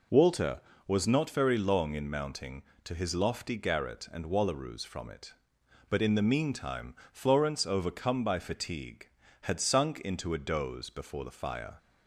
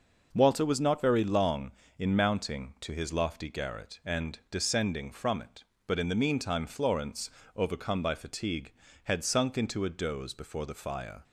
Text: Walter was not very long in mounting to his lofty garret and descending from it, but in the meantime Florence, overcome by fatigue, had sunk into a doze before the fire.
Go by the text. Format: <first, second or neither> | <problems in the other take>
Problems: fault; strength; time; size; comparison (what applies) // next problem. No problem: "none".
second | says "wallaroos" for "descending"; at 4.2 s // pauses between "meantime" and "Florence"; slight; at 6.9 s; 0.18 s long